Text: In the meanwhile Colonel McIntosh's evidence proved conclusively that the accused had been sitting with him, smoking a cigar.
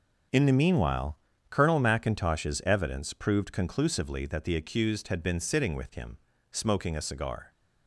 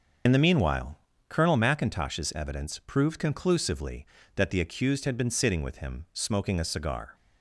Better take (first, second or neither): first